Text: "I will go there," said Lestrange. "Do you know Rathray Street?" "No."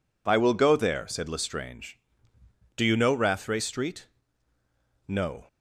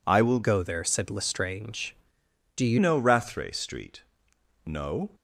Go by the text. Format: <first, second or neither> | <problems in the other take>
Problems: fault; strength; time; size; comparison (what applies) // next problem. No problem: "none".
first | changes voice from "go" to "you"; from 0.4 to 2.7 s; 2.3 s long